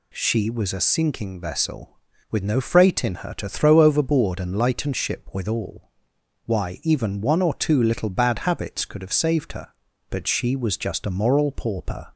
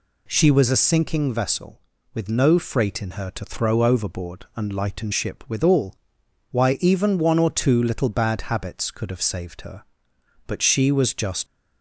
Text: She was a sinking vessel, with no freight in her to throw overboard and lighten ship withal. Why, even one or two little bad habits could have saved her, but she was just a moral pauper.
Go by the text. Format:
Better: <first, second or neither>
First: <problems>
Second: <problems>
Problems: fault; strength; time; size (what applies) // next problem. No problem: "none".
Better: first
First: none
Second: stops before "a moral pauper"; at 11.4 s